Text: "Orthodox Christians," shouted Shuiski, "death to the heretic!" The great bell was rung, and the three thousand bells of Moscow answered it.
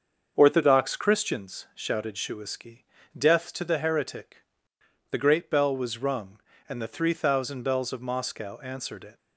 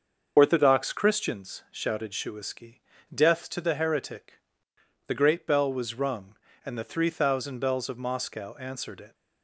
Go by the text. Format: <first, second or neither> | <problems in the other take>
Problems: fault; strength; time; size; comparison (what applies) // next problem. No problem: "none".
first | loses the start of "Orthodox"; at 0.3 s; 30 ms // starts louder than the rest; until 1.3 s; 6.5 dB; also in the first